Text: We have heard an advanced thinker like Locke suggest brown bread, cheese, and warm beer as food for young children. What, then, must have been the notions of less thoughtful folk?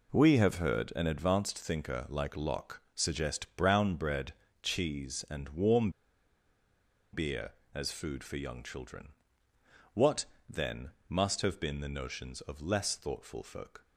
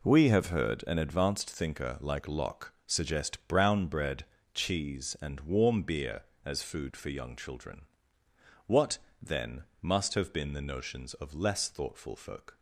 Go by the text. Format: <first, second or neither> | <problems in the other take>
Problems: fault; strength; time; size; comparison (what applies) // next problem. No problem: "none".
second | pauses between "Locke" and "suggest"; slight; at 2.8 s; 0.16 s long; slight in the second // pauses between "warm" and "beer"; at 5.9 s; 1.2 s long